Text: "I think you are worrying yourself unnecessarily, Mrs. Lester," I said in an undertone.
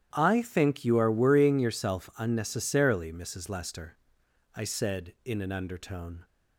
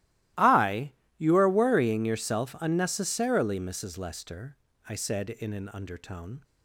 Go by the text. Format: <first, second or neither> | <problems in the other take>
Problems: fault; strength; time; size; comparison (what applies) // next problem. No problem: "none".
first | starts louder than the rest; strong; until 1.6 s; 16.5 dB; strong in the first // skips "think"; at 1.0 s